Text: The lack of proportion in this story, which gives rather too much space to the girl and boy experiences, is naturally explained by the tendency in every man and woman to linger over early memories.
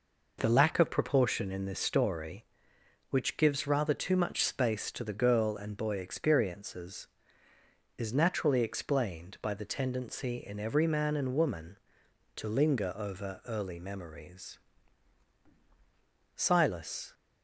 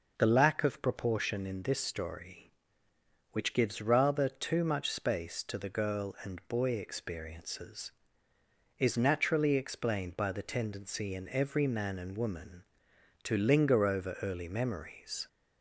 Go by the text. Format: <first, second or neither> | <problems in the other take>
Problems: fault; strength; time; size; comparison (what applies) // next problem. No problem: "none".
second | goes on to say "Silas"; noticeable; from 16.3 s on; 0.76 s long